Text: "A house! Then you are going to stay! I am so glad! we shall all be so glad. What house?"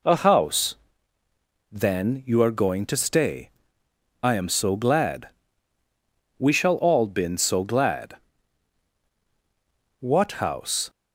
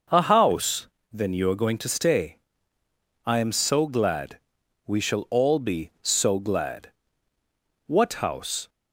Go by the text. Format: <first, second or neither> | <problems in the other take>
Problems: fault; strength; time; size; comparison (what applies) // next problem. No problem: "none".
second | says "been" for "be"; at 7.0 s